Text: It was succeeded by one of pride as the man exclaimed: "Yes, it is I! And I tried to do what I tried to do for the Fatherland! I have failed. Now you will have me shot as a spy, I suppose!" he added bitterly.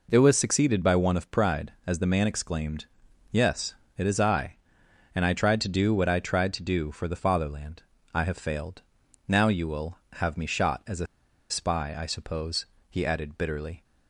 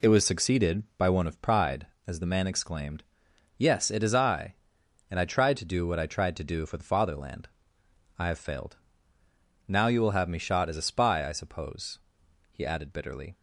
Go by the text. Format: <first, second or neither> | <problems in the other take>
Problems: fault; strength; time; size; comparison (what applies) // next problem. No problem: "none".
second | pauses between "a" and "spy"; at 11.0 s; 0.44 s long